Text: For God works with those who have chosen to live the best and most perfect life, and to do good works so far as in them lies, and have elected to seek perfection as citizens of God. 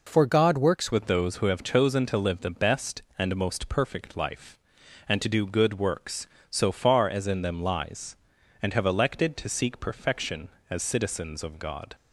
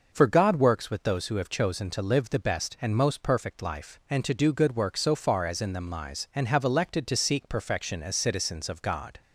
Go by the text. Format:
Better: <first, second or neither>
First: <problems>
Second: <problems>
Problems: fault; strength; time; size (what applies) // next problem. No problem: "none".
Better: second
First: changes voice at "with"; from 0.9 s on; 11.0 s long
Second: none